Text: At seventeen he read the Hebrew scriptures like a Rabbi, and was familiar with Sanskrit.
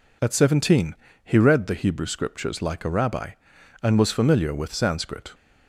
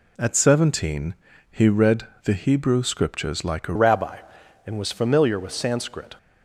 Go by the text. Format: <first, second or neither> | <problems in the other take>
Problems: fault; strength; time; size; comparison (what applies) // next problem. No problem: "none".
first | pauses between "seventeen" and "he"; slight; at 1.1 s; 0.36 s long; slight in the first // pauses between "read" and "the"; slight; at 2.0 s; 0.16 s long // changes voice at "Rabbi"; from 3.7 s on; 2.4 s long